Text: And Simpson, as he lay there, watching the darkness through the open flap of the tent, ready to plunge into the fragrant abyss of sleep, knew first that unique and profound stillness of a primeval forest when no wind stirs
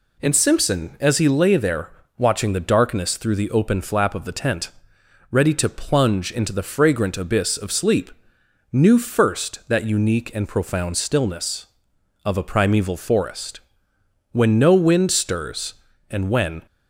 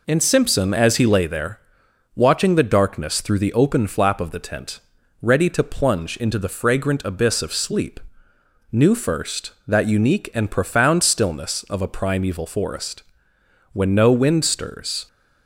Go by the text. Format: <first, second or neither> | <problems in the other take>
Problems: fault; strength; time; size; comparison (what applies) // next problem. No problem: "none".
second | pauses between "forest" and "when"; noticeable; at 13.6 s; 0.72 s long; noticeable in the second // goes on to say "and when"; from 16.0 s on; 0.56 s long